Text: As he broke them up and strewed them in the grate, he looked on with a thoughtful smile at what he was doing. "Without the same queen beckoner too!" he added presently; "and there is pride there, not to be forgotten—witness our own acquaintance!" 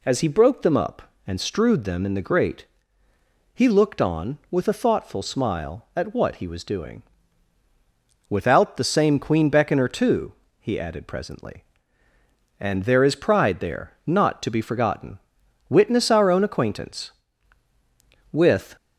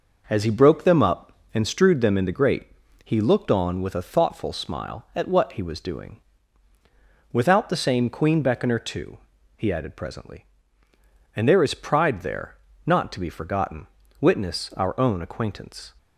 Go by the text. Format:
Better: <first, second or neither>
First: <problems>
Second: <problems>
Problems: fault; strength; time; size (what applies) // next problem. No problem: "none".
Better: second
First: goes on to say "With"; slight; from 18.3 s on; 0.44 s long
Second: none